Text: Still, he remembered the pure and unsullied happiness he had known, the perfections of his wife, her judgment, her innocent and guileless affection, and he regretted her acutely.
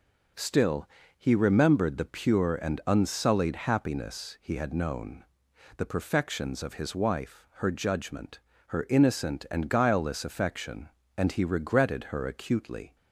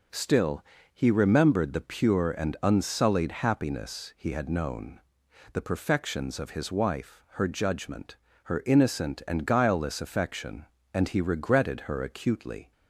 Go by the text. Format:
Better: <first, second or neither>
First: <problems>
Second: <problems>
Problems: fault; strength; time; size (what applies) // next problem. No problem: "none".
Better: neither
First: none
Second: none